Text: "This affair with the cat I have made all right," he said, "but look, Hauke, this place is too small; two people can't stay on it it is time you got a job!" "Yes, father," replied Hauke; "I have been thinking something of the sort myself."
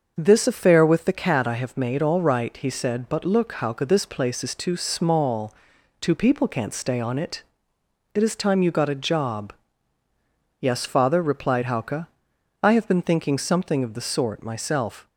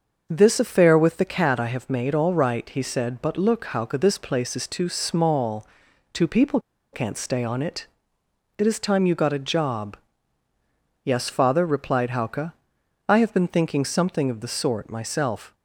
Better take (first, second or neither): first